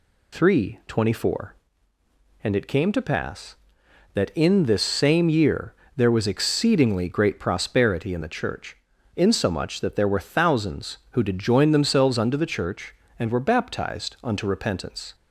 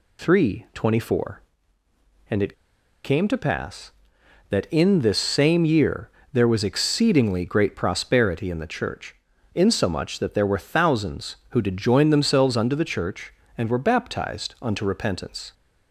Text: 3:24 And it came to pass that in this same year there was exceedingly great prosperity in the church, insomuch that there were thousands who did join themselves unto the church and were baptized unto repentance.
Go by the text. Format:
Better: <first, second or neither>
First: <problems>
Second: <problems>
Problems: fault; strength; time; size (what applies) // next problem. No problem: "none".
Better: first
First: pauses between "year" and "there"; slight; at 5.7 s; 0.19 s long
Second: pauses between "it" and "came"; noticeable; at 2.5 s; 0.52 s long // pauses between "year" and "there"; slight; at 6.1 s; 0.20 s long